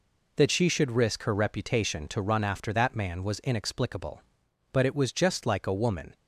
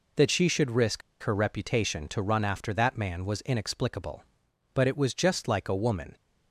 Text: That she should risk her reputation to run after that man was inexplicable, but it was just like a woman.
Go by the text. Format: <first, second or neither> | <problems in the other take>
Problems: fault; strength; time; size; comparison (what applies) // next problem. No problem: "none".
first | pauses between "risk" and "her"; slight; at 1.0 s; 0.22 s long